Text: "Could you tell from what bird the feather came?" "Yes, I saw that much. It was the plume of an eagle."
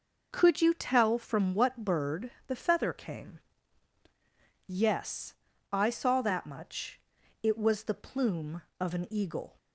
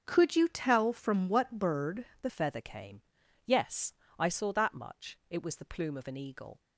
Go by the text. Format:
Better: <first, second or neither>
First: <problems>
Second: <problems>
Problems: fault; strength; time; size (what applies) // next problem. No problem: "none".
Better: first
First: pauses between "bird" and "the"; slight; at 2.3 s; 0.16 s long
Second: starts louder than the rest; strong; until 1.0 s; 7.5 dB // pauses between "bird" and "the"; slight; at 2.0 s; 0.16 s long // changes voice at "feather"; from 2.2 s on; 4.3 s long